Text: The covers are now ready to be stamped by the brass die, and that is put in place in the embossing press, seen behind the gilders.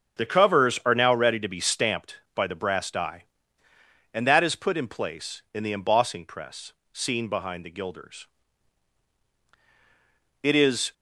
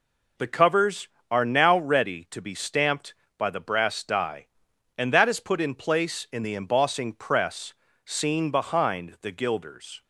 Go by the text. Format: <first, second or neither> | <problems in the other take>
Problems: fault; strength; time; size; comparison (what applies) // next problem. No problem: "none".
second | starts louder than the rest; until 1.2 s; 6.5 dB // goes on to say "It is"; from 10.4 s on; 0.52 s long